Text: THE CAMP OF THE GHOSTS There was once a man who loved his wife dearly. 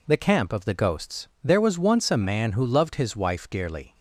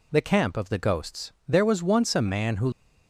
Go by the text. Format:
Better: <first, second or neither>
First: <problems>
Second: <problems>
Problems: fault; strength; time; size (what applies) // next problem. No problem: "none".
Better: first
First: pauses between "GHOSTS" and "There"; slight; at 1.2 s; 0.16 s long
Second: pauses between "GHOSTS" and "There"; slight; at 1.3 s; 0.16 s long // stops before "loved his wife dearly"; at 2.7 s